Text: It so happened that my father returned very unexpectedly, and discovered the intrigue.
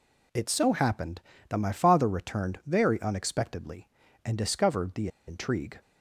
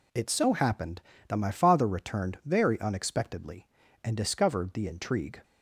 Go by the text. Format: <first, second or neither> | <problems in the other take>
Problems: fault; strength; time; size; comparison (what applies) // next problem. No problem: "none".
second | pauses between "the" and "intrigue"; slight; at 5.0 s; 0.20 s long